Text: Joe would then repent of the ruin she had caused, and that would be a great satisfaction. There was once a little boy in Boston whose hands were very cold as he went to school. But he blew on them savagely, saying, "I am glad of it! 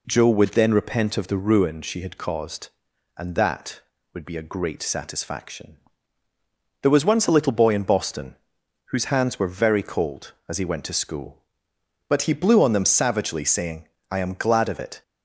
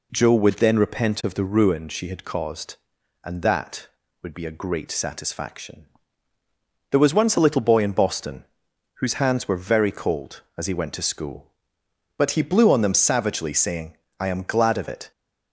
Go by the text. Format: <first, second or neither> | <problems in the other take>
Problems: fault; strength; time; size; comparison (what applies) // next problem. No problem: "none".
neither | pauses between "Boston" and "whose"; noticeable; the same in both